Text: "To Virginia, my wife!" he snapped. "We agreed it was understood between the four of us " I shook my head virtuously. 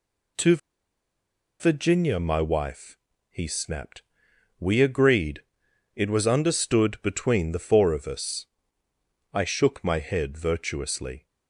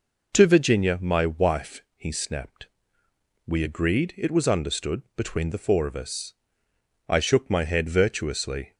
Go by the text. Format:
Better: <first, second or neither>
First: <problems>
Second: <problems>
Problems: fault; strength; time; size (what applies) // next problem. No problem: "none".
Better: second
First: pauses between "To" and "Virginia"; at 0.5 s; 1.0 s long // pauses between "agreed" and "it"; noticeable; at 5.4 s; 0.52 s long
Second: none